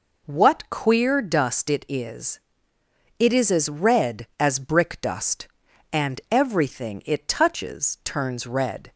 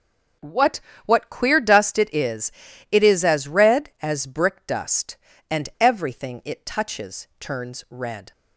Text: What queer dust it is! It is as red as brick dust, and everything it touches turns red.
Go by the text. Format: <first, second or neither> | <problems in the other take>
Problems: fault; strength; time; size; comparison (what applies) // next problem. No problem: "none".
first | starts louder than the rest; until 1.6 s; 6 dB // says "What" twice; at 1.0 s